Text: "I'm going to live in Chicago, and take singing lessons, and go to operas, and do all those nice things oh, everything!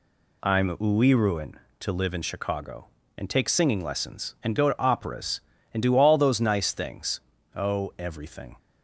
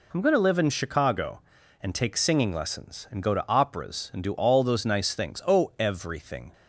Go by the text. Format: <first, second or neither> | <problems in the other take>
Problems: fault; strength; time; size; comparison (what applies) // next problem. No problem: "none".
second | says "uiruin" for "going"; at 0.7 s // pauses between "things" and "oh"; slight; at 7.1 s; 0.36 s long